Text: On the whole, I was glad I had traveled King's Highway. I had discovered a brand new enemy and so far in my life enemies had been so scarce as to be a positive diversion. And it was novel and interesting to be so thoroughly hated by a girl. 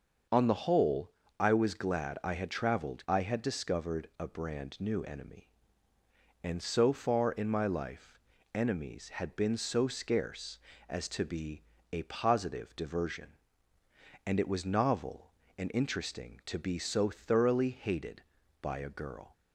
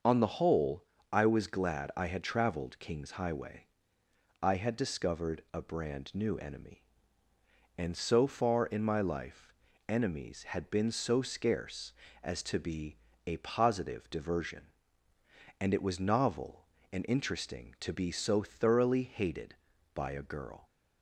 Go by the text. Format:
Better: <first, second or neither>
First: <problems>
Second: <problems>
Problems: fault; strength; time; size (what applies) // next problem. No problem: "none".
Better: second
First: starts louder than the rest; until 1.6 s; 6.5 dB // skips "King's Highway"; at 3.0 s // pauses between "life" and "enemies"; slight; at 8.1 s; 0.34 s long // pauses between "be" and "a"; slight; at 11.6 s; 0.30 s long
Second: starts louder than the rest; until 1.3 s; 6.5 dB // pauses between "life" and "enemies"; slight; at 9.5 s; 0.34 s long // pauses between "be" and "a"; slight; at 12.9 s; 0.30 s long